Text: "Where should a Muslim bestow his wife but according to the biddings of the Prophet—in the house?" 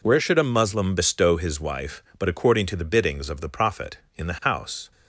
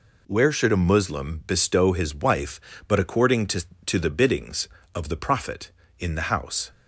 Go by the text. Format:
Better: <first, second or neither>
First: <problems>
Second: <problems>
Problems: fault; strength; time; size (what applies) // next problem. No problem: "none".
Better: first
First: none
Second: says "to" twice; at 3.8 s